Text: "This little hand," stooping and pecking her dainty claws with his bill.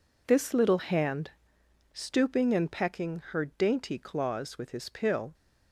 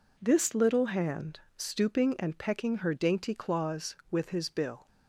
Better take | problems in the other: second | says "pill" for "bill"; at 4.8 s

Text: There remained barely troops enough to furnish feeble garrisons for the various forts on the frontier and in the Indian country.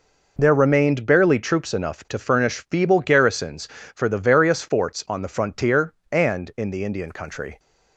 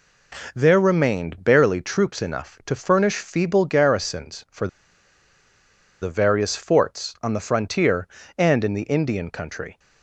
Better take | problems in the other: first | pauses between "for" and "the"; strong; at 4.6 s; 1.3 s long

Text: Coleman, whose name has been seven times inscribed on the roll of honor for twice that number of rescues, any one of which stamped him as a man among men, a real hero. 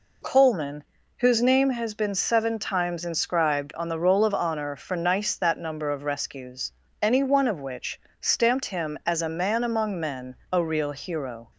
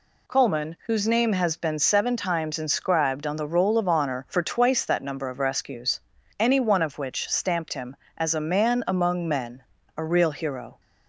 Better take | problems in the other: second | says "nice" for "twice"; at 4.9 s // pauses between "which" and "stamped"; slight; at 7.9 s; 0.22 s long

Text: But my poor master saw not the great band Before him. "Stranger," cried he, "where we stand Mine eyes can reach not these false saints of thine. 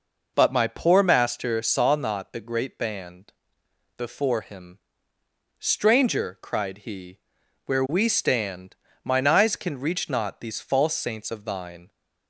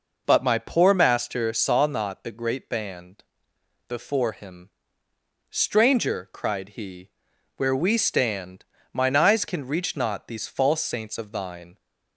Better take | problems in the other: neither | pauses between "band" and "Before"; noticeable; the same in both // pauses between "stand" and "Mine"; slight; the same in both

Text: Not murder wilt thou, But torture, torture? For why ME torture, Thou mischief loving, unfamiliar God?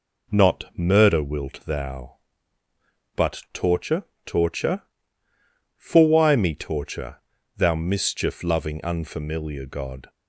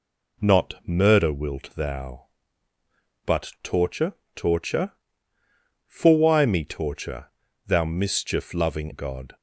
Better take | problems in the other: first | skips "unfamiliar"; at 8.9 s

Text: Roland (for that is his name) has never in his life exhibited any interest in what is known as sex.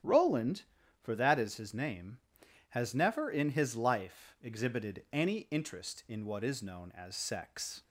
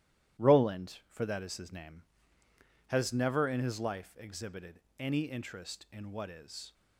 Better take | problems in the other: first | starts louder than the rest; strong; until 1.5 s; 13 dB; strong in the first // pauses between "exhibited" and "any"; slight; at 4.7 s; 0.20 s long // stops before "known as sex"; at 6.7 s

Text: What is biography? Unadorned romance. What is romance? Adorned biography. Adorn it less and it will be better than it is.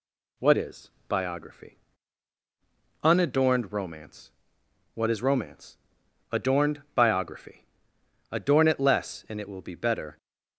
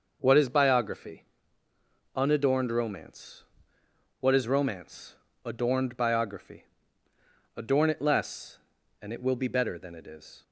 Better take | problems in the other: second | pauses between "is" and "biography"; slight; at 0.9 s; 0.16 s long // stops before "than it is"; at 10.1 s

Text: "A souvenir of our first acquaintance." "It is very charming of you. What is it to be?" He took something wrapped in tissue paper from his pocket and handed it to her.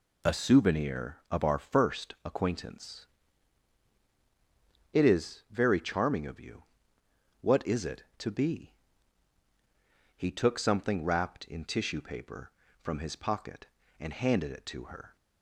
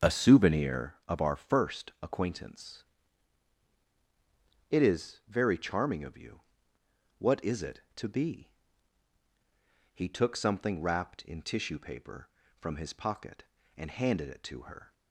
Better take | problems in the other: first | starts louder than the rest; until 0.9 s; 6.5 dB

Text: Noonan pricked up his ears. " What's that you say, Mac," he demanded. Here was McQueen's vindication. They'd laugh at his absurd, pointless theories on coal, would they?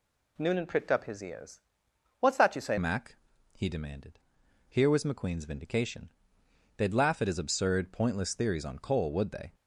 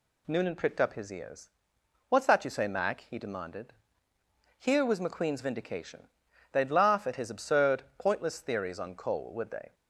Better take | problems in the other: second | changes voice at "Mac"; from 2.7 s on; 6.8 s long

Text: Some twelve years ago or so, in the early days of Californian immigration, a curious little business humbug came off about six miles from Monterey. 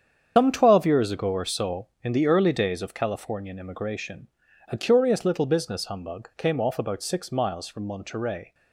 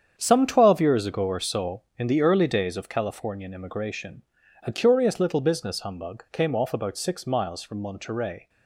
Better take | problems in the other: second | loses the start of "Some"; at 0.3 s; 120 ms // starts louder than the rest; strong; until 1.3 s; 8 dB; strong in the second

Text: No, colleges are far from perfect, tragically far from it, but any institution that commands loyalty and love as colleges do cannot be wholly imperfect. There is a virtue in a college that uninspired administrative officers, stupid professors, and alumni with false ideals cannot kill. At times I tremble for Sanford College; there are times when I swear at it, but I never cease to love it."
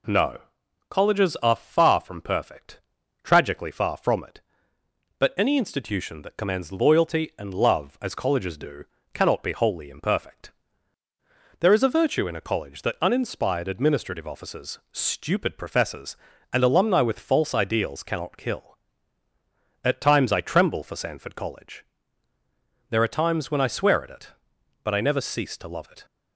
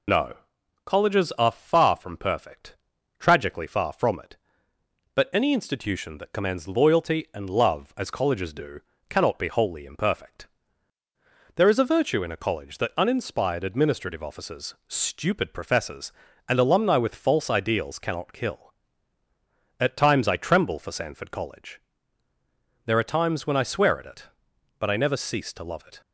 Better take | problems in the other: first | loses the start of "No"; at 0.0 s; 85 ms // pauses between "do" and "cannot"; slight; at 8.7 s; 0.32 s long; slight in the first

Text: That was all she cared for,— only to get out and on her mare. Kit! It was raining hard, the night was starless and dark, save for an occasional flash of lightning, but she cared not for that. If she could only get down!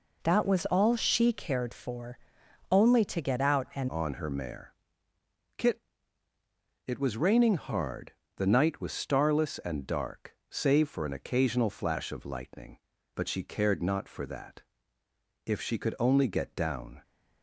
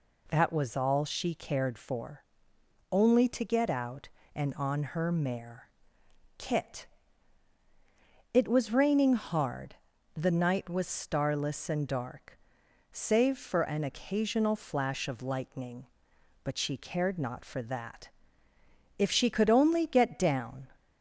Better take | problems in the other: second | changes voice at "on"; from 3.8 s on; 13.2 s long

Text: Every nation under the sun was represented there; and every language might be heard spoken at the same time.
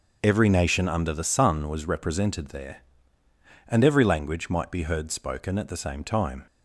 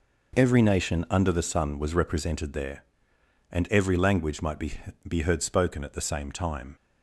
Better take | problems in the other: first | says "be" twice; at 5.0 s

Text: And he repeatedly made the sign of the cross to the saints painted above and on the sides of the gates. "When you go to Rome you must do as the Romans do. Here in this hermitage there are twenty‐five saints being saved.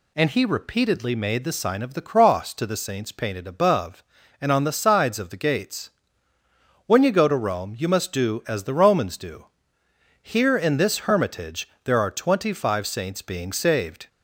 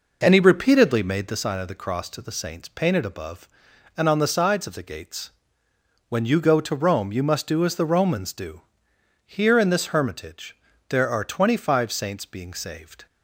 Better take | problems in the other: first | starts louder than the rest; noticeable; until 1.5 s; 5 dB // pauses between "hermitage" and "there"; slight; at 10.5 s; 0.34 s long; slight in the first

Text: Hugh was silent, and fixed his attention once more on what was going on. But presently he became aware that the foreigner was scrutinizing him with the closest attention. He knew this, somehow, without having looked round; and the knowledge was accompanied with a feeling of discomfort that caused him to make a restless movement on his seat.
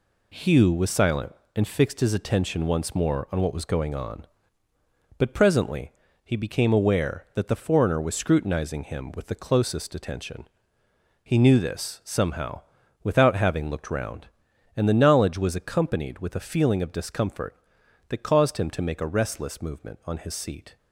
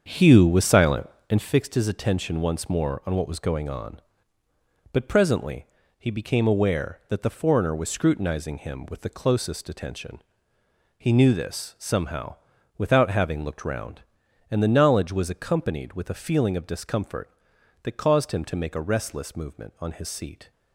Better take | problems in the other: first | starts louder than the rest; strong; until 1.5 s; 7 dB // pauses between "presently" and "he"; slight; at 5.6 s; 0.32 s long; slight in the first

